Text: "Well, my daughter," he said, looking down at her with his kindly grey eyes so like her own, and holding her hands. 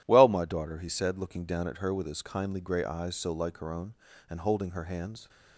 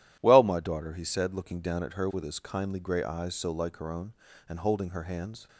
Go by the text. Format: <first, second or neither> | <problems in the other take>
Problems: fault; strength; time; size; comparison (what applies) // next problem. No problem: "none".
neither | none